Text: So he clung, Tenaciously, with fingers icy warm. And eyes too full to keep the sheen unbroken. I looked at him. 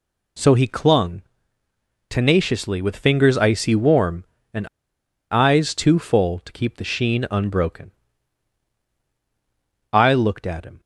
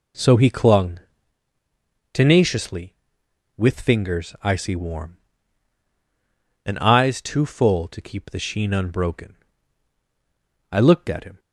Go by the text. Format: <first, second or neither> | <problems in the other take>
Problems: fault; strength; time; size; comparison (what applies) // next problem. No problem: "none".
second | pauses between "And" and "eyes"; noticeable; at 4.6 s; 0.63 s long